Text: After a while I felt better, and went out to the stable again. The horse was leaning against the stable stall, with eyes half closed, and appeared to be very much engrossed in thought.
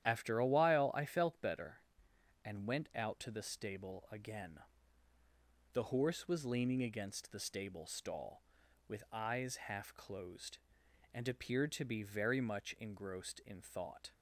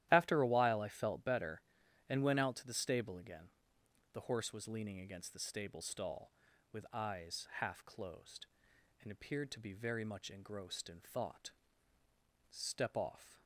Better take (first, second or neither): first